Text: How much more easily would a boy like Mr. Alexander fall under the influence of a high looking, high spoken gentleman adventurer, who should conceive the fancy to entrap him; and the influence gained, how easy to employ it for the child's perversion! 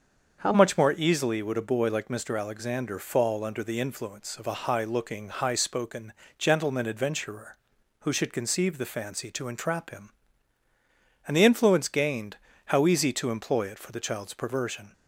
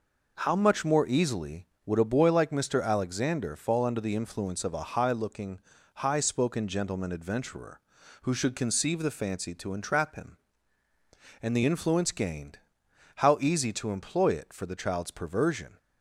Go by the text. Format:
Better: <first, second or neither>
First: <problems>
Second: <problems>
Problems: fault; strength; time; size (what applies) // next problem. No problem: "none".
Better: second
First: starts louder than the rest; until 1.4 s; 6.5 dB // changes voice at "much"; from 0.5 s on; 14.4 s long // pauses between "spoken" and "gentleman"; slight; at 6.1 s; 0.24 s long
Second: none